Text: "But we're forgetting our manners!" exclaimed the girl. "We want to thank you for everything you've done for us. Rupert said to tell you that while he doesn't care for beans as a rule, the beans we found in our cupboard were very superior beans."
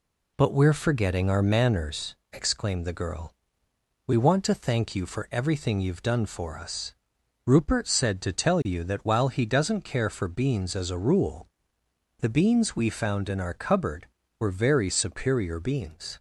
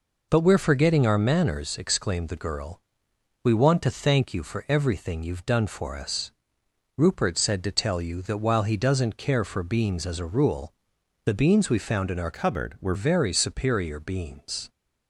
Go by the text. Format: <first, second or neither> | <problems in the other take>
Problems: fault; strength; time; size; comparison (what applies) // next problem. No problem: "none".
first | changes voice from "cupboard" to "were"; from 12.3 to 12.9 s; 0.6 s long